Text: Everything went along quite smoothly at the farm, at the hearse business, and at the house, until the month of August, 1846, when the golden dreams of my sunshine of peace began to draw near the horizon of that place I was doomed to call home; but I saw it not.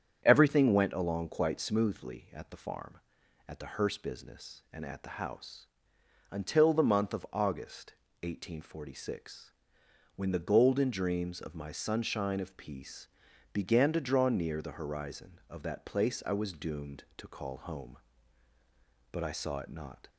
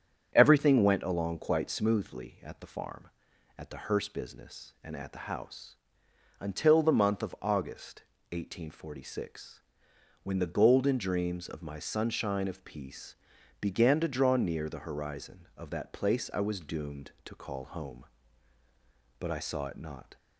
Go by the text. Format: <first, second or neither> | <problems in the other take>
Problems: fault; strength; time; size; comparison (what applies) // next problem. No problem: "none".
neither | starts louder than the rest; strong; the same in both // pauses between "peace" and "began"; noticeable; the same in both